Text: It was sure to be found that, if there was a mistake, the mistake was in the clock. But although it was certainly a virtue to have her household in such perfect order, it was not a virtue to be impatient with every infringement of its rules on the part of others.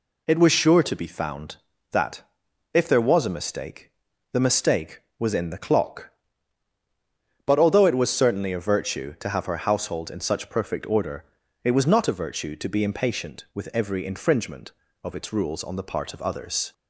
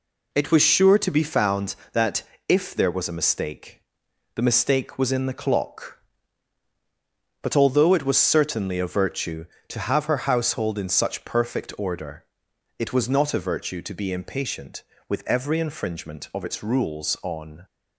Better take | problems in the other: first | stops before "the part of others"; at 17.6 s

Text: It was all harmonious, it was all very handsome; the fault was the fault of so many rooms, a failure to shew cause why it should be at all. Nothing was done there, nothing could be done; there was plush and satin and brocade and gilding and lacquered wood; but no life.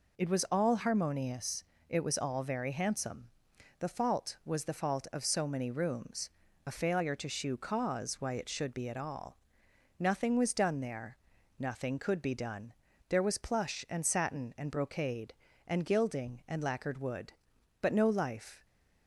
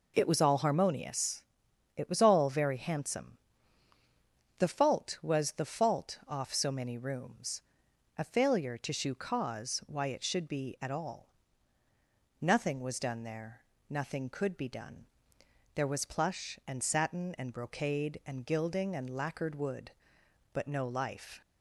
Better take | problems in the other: first | says "off" for "of"; at 6.2 s

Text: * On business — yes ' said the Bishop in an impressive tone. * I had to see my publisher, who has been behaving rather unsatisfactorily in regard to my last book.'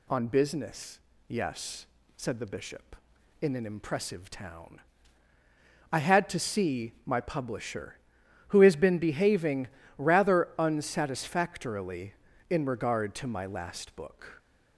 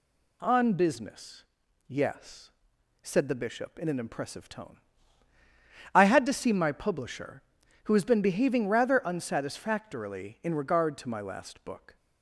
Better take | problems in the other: second | says "town" for "tone"; at 4.3 s // pauses between "behaving" and "rather"; slight; at 9.6 s; 0.32 s long

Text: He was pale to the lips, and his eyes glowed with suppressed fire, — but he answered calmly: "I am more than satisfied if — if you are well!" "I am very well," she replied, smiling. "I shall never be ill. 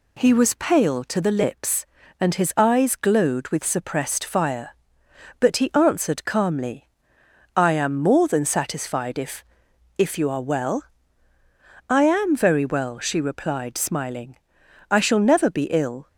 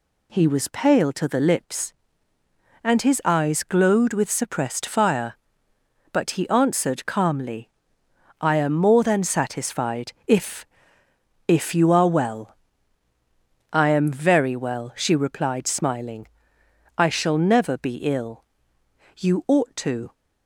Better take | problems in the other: first | pauses between "satisfied" and "if"; slight; at 10.1 s; 0.16 s long // goes on to say "You ought to"; noticeable; from 19.1 s on; 0.96 s long

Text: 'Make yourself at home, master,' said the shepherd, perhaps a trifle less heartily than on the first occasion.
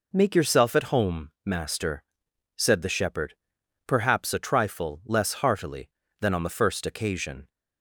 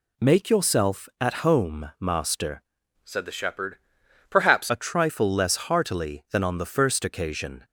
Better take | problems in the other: first | changes voice from "said" to "perhaps"; from 3.0 to 4.6 s; 1.6 s long

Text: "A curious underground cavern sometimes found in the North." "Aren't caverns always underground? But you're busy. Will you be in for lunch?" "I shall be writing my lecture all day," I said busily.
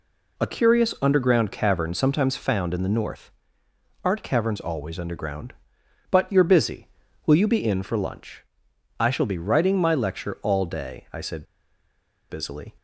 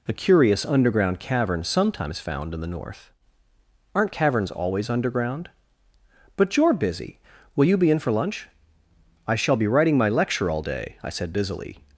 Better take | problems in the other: second | pauses between "said" and "busily"; noticeable; at 11.4 s; 0.84 s long

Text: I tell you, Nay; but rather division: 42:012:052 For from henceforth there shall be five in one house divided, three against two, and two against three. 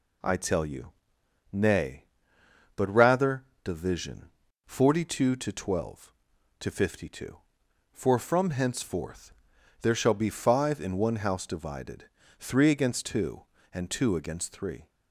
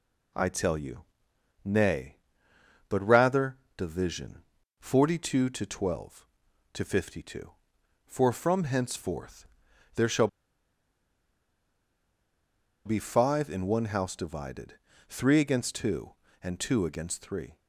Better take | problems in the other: first | pauses between "rather" and "division"; slight; at 3.5 s; 0.18 s long; slight in the first // pauses between "henceforth" and "there"; noticeable; at 9.4 s; 0.50 s long; noticeable in the first // pauses between "shall" and "be"; strong; at 10.2 s; 2.5 s long

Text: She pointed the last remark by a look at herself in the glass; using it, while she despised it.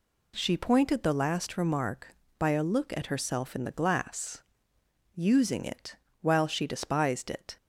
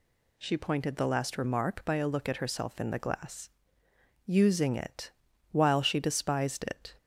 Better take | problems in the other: neither | none

